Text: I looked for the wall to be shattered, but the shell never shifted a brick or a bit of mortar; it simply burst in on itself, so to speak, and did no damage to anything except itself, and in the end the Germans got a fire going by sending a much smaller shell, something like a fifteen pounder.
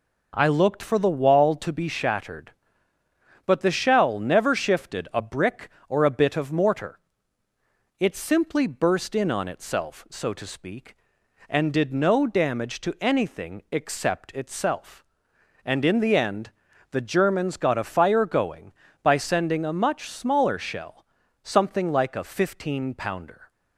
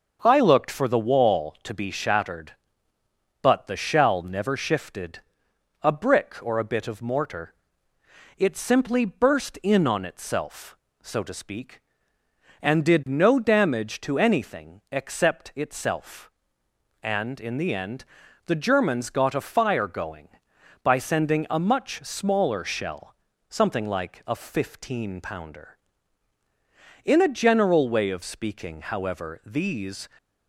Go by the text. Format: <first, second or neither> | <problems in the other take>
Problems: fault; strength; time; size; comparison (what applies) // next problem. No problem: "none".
first | starts louder than the rest; until 1.2 s; 6.5 dB // pauses between "shifted" and "a"; noticeable; at 5.2 s; 0.60 s long // pauses between "end" and "the"; at 18.0 s; 0.40 s long; also in the first // goes on to say "In a general way of speaking however these"; strong; from 27.0 s on; 3.0 s long